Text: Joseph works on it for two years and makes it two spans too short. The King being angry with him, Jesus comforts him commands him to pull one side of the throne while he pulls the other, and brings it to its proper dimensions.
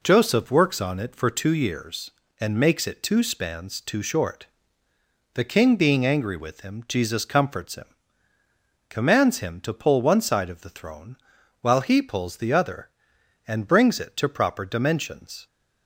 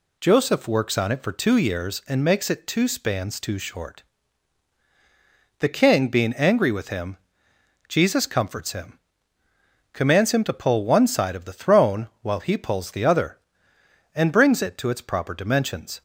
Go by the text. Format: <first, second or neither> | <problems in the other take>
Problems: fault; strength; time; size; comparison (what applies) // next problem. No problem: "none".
second | pauses between "him" and "commands"; at 7.8 s; 1.0 s long; also in the second // pauses between "throne" and "while"; noticeable; at 11.1 s; 0.46 s long // skips "its"; at 14.2 s